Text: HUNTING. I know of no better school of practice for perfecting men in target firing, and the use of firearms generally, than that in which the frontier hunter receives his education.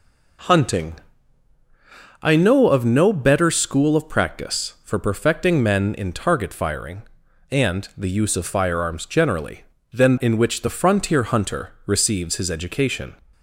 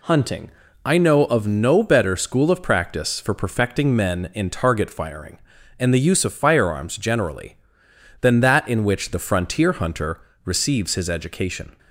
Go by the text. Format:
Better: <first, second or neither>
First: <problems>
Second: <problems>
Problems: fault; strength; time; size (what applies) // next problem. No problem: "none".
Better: second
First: skips "that"; at 10.1 s // pauses between "hunter" and "receives"; slight; at 11.7 s; 0.16 s long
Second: pauses between "hunter" and "receives"; slight; at 10.1 s; 0.24 s long